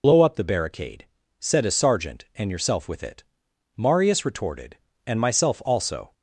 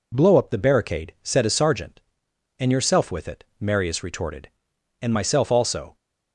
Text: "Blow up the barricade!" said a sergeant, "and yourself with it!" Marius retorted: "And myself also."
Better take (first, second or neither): second